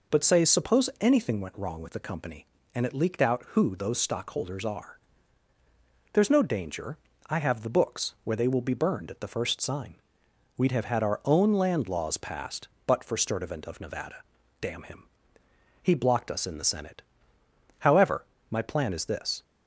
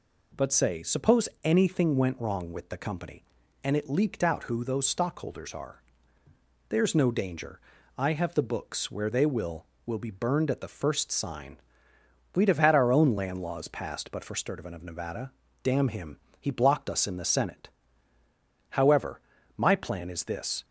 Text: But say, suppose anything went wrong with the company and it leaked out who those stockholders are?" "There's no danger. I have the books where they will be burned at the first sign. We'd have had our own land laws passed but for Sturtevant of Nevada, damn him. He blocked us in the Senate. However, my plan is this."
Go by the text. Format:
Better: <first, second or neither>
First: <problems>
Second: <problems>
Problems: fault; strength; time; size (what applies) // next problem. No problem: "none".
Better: first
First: none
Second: says "will" twice; at 9.8 s